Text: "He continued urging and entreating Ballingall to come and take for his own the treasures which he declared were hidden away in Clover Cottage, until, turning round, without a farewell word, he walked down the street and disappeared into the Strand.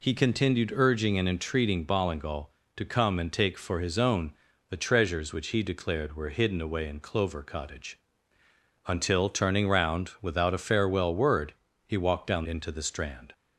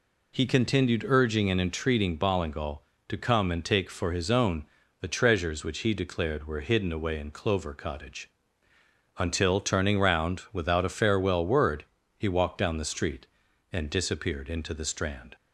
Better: second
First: pauses between "own" and "the"; slight; at 4.3 s; 0.34 s long // skips "the street and disappeared"; at 12.4 s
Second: pauses between "own" and "the"; slight; at 4.6 s; 0.32 s long

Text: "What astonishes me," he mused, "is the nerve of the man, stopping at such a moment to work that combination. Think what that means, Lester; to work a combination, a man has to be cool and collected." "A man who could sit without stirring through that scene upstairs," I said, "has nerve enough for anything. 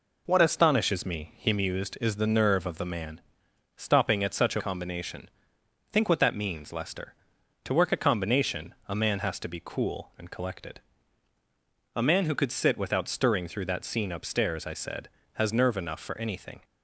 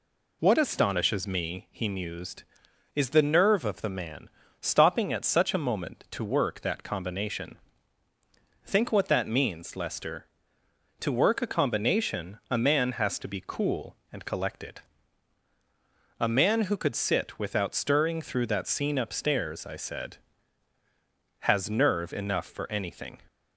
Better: second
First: skips "moment to work that"; at 4.6 s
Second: none

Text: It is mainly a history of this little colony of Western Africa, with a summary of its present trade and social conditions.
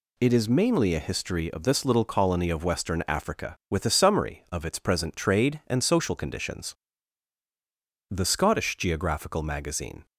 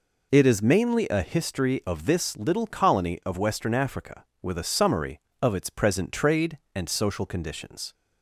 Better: second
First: goes on to say "The Scottish Geographical Magazine"; strong; from 8.0 s on; 1.9 s long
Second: none

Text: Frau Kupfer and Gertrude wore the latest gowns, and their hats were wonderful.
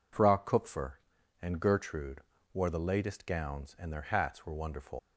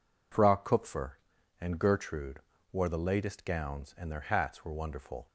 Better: second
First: pauses between "Gertrude" and "wore"; slight; at 2.1 s; 0.34 s long // leaves "wonderful" unfinished; at 4.9 s; 85 ms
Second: pauses between "Gertrude" and "wore"; slight; at 2.3 s; 0.34 s long

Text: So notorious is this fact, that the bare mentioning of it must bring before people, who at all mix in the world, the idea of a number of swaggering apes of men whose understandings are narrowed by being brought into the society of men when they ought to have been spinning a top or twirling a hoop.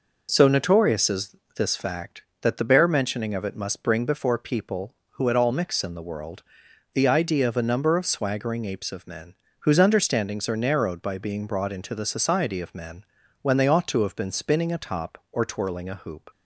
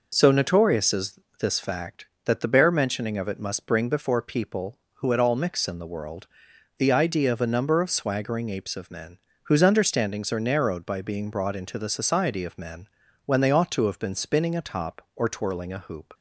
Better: neither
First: pauses between "is" and "this"; slight; at 1.3 s; 0.20 s long // pauses between "men" and "whose"; slight; at 9.3 s; 0.28 s long // pauses between "men" and "when"; slight; at 13.0 s; 0.36 s long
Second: pauses between "is" and "this"; slight; at 1.1 s; 0.20 s long // pauses between "men" and "whose"; slight; at 9.1 s; 0.28 s long // pauses between "men" and "when"; slight; at 12.8 s; 0.36 s long

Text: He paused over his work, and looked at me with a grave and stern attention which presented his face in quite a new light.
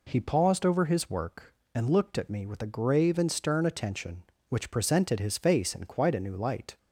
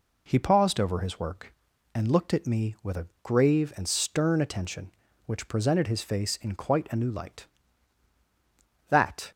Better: first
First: none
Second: pauses between "a" and "grave"; slight; at 3.0 s; 0.16 s long // goes on to say "That"; slight; from 8.8 s on; 0.42 s long

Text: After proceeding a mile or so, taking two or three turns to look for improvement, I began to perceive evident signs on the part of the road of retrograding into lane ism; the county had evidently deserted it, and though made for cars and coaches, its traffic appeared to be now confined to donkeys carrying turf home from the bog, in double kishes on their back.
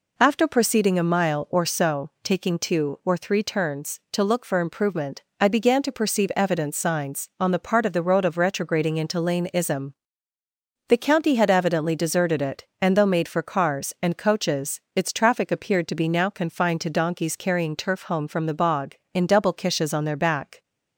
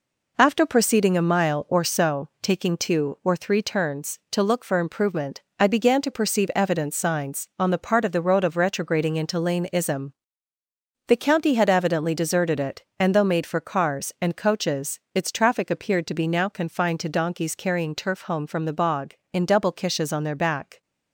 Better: first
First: none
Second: gets quieter; noticeable; throughout; 5.5 dB

